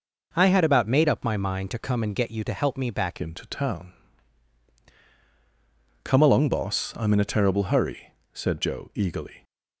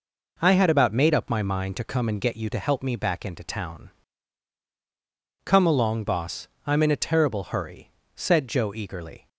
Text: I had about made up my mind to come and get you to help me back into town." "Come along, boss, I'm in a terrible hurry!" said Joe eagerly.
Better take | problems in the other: second | changes voice at "into"; from 3.1 s on; 6.3 s long

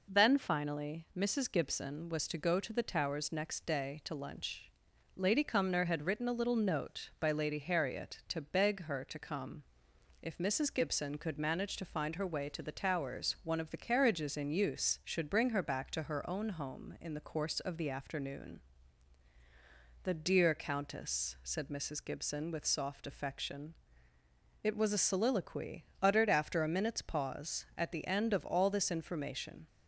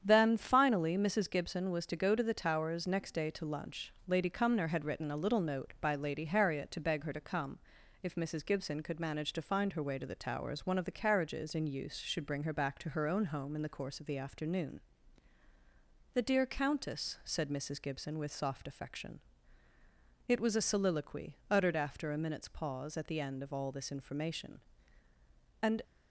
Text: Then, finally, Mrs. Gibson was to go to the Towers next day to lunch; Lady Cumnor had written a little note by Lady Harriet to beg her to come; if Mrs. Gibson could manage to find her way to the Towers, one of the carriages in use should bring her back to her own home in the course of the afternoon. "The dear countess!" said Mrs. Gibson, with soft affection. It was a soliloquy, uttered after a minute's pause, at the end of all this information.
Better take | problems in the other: first | starts louder than the rest; strong; until 1.0 s; 8.5 dB // goes on to say "And"; slight; from 25.6 s on; 0.20 s long

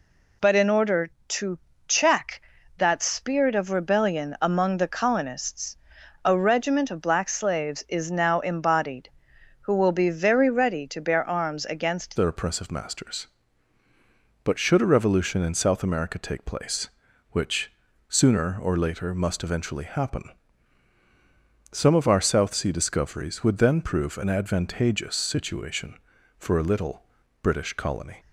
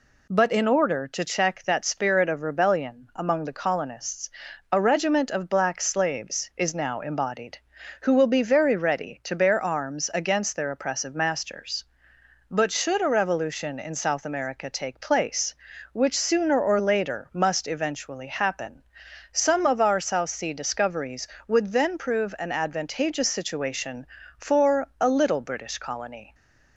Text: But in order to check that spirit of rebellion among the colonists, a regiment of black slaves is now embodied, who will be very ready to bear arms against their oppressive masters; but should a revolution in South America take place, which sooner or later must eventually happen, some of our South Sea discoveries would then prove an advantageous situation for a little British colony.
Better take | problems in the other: second | pauses between "to" and "check"; slight; at 1.5 s; 0.30 s long // changes voice at "their"; from 12.1 s on; 16.0 s long // pauses between "which" and "sooner"; at 17.7 s; 0.38 s long // pauses between "little" and "British"; slight; at 27.0 s; 0.36 s long

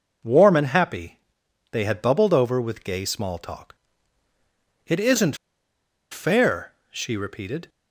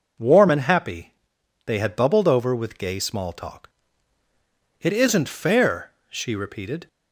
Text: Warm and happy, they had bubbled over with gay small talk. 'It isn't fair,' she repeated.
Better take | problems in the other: second | pauses between "isn't" and "fair"; noticeable; at 5.3 s; 0.74 s long

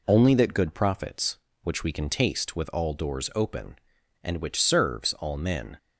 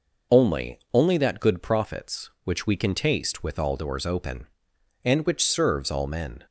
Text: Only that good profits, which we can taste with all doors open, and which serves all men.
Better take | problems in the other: first | says "Only" twice; at 0.9 s

